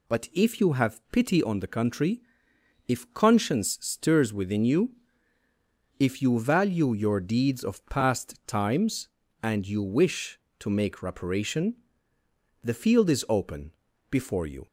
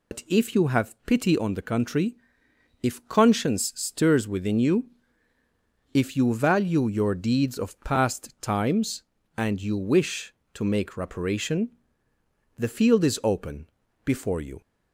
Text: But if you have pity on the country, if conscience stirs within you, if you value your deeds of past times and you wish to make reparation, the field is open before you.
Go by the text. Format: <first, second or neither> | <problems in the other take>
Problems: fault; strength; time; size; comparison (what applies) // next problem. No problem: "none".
first | loses the start of "But"; at 0.1 s; 85 ms // pauses between "open" and "before"; at 13.6 s; 0.38 s long; also in the first